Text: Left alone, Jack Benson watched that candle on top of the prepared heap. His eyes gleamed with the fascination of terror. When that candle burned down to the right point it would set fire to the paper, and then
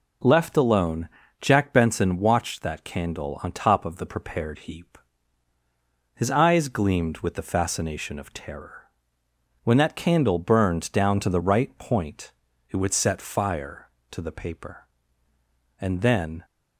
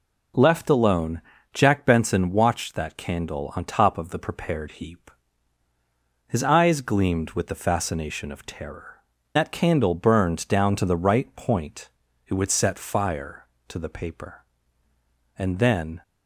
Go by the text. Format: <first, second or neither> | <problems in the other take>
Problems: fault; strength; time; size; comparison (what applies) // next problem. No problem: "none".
first | skips "When"; at 9.1 s // pauses between "point" and "it"; slight; at 11.8 s; 0.36 s long; slight in the first